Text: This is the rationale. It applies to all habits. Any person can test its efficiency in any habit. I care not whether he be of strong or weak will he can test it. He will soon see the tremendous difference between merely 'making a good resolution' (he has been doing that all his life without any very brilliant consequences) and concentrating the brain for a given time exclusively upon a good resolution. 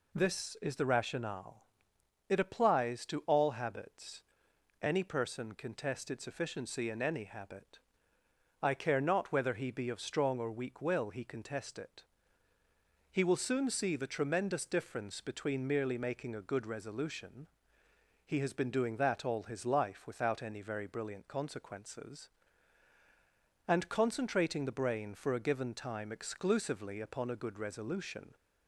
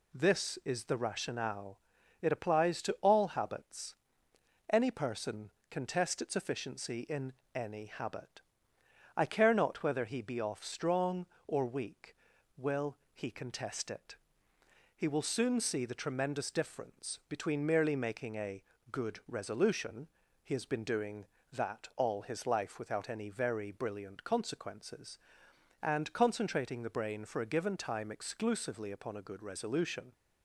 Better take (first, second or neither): first